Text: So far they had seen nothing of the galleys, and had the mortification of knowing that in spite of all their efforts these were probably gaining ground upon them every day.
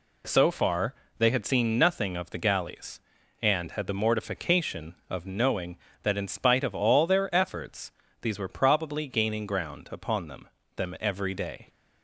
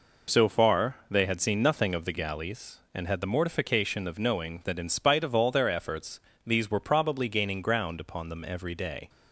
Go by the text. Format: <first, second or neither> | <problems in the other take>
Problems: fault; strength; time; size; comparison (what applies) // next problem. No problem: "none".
second | pauses between "far" and "they"; slight; at 0.9 s; 0.26 s long // pauses between "efforts" and "these"; slight; at 7.9 s; 0.30 s long; slight in the second // says "them" twice; at 10.7 s